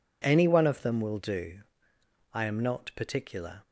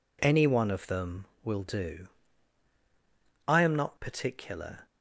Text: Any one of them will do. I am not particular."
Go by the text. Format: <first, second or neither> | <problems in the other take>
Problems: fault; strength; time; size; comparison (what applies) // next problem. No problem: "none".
neither | none